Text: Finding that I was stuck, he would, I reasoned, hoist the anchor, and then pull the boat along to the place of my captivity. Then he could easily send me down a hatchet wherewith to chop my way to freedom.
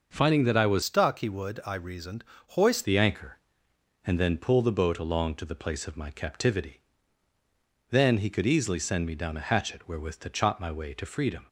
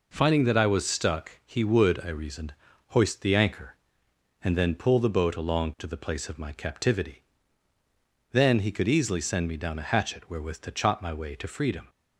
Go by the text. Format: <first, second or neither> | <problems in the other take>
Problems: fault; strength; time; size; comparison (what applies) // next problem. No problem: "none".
second | changes voice from "stuck" to "hoist"; from 0.8 to 2.8 s; 2.0 s long